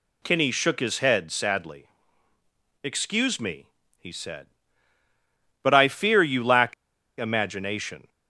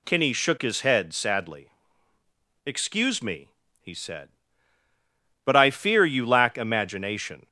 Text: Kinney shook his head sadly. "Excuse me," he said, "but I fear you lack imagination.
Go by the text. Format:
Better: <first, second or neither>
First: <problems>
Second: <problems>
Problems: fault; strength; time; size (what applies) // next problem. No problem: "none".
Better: second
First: pauses between "lack" and "imagination"; noticeable; at 6.7 s; 0.46 s long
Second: none